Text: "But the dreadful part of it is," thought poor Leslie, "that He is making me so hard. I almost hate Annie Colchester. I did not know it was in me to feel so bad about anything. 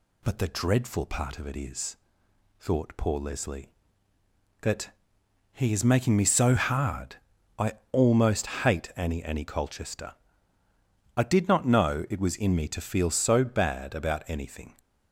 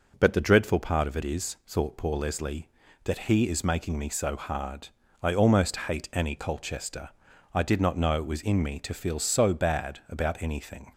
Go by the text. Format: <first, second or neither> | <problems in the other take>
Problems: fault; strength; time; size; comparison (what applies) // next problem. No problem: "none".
second | pauses between "that" and "He"; noticeable; at 4.8 s; 0.62 s long // pauses between "I" and "almost"; slight; at 7.7 s; 0.18 s long // pauses between "almost" and "hate"; slight; at 8.4 s; 0.16 s long // says "Annie" twice; at 9.2 s